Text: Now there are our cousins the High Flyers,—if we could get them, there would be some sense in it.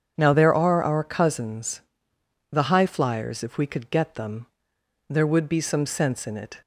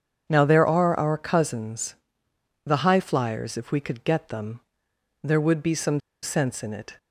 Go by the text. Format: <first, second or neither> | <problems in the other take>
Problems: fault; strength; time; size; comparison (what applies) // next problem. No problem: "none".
first | starts louder than the rest; strong; until 1.2 s; 7 dB; strong in the first // pauses between "cousins" and "the"; noticeable; at 1.9 s; 0.72 s long; noticeable in the first // pauses between "some" and "sense"; slight; at 5.9 s; 0.23 s long